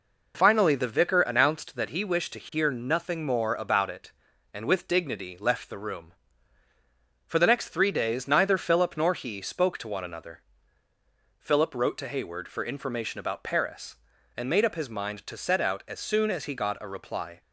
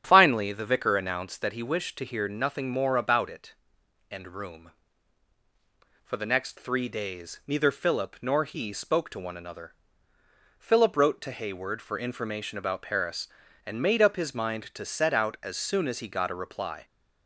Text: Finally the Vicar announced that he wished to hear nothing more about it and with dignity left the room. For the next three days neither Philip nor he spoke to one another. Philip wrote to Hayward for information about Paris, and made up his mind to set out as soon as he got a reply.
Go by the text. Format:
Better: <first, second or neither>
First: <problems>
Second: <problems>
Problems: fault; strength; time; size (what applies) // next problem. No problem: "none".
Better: first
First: none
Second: starts louder than the rest; strong; until 1.0 s; 8.5 dB // skips "with dignity left the"; at 4.2 s